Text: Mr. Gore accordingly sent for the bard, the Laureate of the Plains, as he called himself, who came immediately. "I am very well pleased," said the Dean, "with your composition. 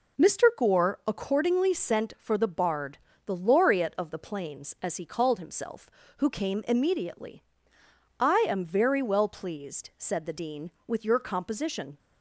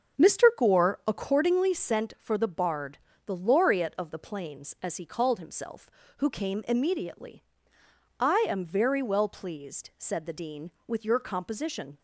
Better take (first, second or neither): first